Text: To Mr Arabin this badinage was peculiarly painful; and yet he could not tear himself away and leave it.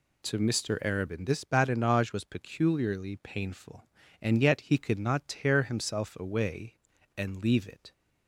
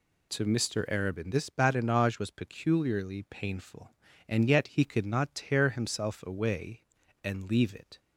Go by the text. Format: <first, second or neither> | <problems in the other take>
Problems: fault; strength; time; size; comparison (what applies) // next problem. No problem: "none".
neither | none